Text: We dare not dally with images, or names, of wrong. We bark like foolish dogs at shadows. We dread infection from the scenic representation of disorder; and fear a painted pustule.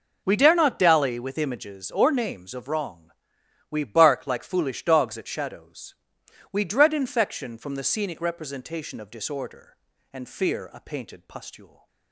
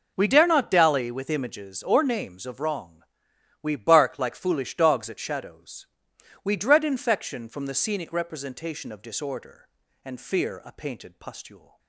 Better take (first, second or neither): neither